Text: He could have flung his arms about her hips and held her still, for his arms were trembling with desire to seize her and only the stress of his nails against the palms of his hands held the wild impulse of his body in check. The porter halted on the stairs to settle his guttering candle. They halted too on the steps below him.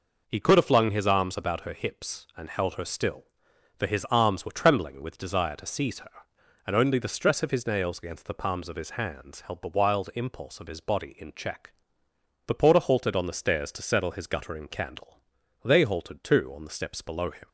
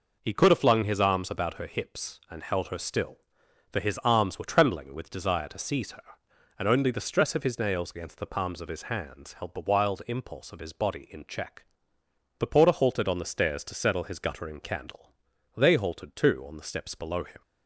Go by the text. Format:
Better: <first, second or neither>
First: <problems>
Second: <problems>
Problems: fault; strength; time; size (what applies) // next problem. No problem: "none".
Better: neither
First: none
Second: none